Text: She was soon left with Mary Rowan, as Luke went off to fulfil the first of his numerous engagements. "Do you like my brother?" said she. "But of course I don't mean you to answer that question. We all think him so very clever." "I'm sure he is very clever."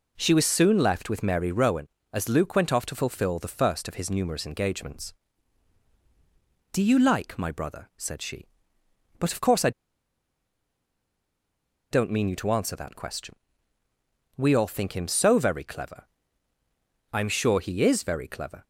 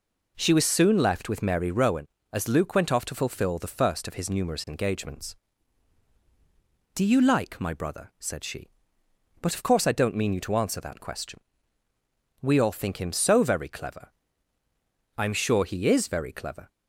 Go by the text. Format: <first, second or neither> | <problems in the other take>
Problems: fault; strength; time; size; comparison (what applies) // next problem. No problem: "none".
second | pauses between "I" and "don't"; strong; at 9.7 s; 2.2 s long